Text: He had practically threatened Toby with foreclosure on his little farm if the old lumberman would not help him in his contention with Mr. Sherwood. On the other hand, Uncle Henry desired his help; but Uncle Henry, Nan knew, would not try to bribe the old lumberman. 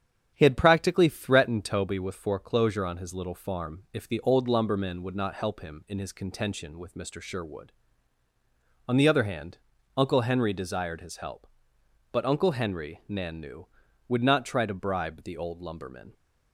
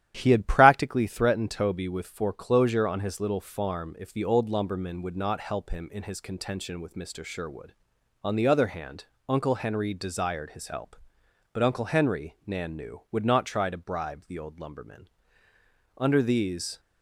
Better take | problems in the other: first | starts louder than the rest; strong; until 1.1 s; 11 dB; strong in the first // goes on to say "Under these"; noticeable; from 15.9 s on; 0.82 s long

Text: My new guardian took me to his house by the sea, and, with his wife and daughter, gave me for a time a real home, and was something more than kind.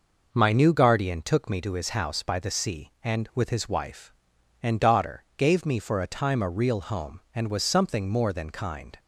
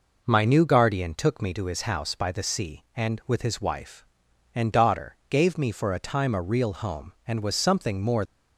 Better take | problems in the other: first | stops before "than kind"; at 8.2 s

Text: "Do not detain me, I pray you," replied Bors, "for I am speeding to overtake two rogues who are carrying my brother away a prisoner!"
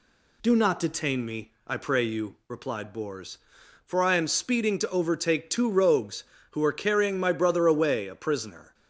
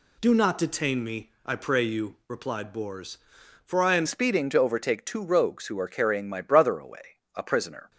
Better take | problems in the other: first | changes voice at "speeding"; from 4.0 s on; 3.9 s long // pauses between "away" and "a"; slight; at 7.1 s; 0.16 s long

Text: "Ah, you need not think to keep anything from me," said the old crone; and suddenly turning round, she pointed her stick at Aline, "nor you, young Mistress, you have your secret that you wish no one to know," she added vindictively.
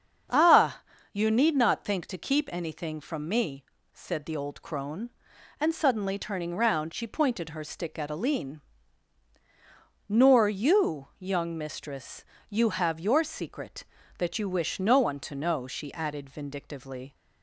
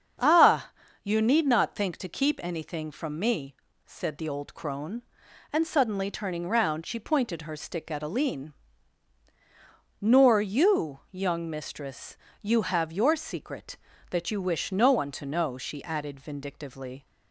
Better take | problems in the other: neither | starts louder than the rest; the same in both

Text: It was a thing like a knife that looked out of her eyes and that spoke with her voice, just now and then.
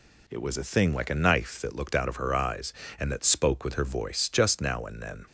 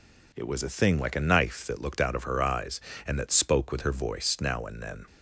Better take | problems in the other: first | skips "just"; at 4.3 s

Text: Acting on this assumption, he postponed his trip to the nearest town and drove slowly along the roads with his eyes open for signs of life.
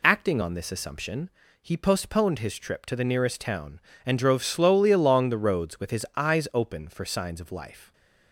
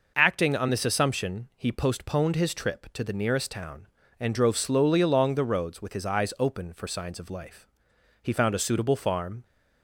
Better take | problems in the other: first | goes on to say "He found a suitable farm"; noticeable; from 8.2 s on; 1.2 s long

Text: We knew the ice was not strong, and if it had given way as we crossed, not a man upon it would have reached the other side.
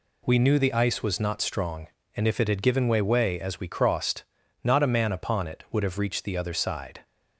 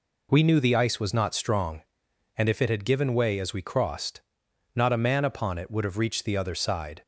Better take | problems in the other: second | says "way" twice; at 3.0 s

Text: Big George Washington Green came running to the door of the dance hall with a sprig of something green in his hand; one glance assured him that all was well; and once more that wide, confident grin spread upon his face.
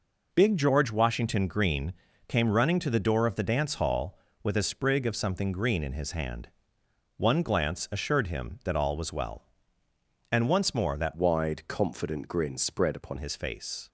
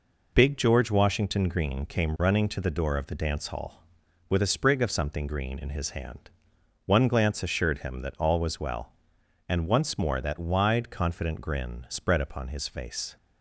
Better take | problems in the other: second | pauses between "Green" and "came"; slight; at 1.9 s; 0.36 s long // changes voice from "wide" to "upon"; from 11.1 to 13.1 s; 2.0 s long

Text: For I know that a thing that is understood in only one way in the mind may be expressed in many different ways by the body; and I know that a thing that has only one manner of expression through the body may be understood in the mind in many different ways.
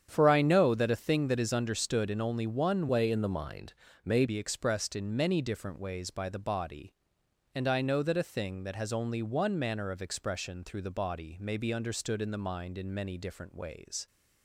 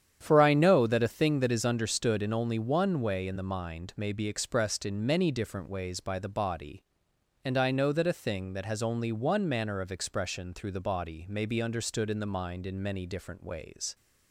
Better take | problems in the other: second | starts louder than the rest; strong; until 1.1 s; 8.5 dB; strong in the second // changes voice from "way" to "may"; from 2.8 to 4.2 s; 1.4 s long // pauses between "mind" and "may"; slight; at 3.7 s; 0.32 s long

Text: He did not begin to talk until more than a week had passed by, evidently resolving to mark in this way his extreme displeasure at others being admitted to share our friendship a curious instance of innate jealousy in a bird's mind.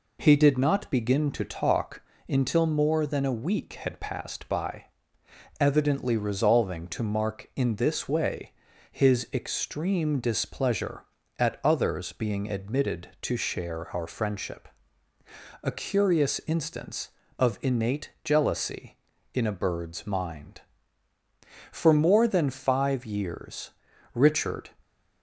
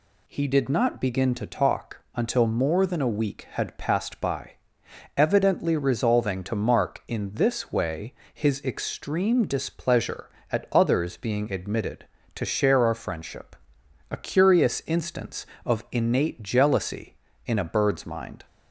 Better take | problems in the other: second | pauses between "talk" and "until"; slight; at 2.0 s; 0.26 s long // pauses between "way" and "his"; at 8.5 s; 0.40 s long; slight in the second // pauses between "friendship" and "a"; noticeable; at 14.6 s; 0.94 s long; noticeable in the second // goes on to say "For more than five years Richard"; strong; from 21.7 s on; 2.9 s long

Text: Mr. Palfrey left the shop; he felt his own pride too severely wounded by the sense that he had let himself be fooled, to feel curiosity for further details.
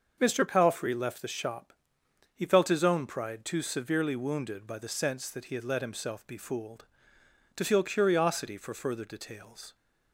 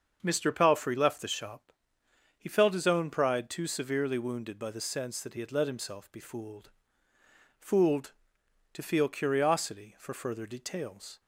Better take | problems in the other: first | starts louder than the rest; until 1.2 s; 6.5 dB; also in the first // says "fooled" twice; at 7.5 s

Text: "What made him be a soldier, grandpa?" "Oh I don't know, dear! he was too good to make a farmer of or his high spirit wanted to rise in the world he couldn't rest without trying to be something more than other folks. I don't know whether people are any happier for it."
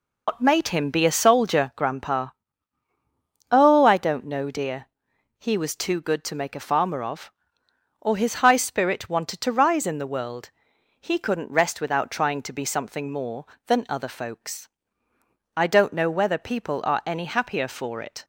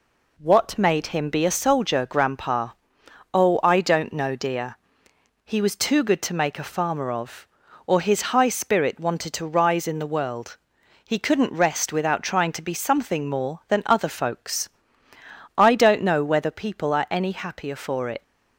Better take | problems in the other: second | loses the start of "What"; at 0.2 s; 115 ms // pauses between "world" and "he"; noticeable; at 10.5 s; 0.50 s long; also in the second

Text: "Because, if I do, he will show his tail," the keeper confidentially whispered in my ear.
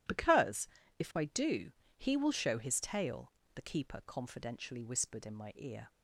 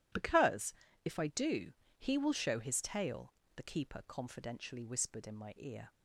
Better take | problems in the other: neither | none

